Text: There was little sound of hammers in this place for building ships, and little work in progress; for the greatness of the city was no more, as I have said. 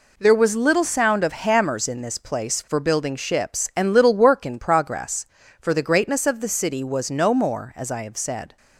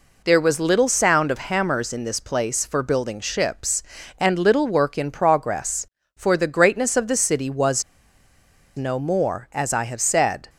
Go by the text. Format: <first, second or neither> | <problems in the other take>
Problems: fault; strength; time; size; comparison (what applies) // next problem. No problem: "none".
first | pauses between "was" and "no"; noticeable; at 7.8 s; 0.93 s long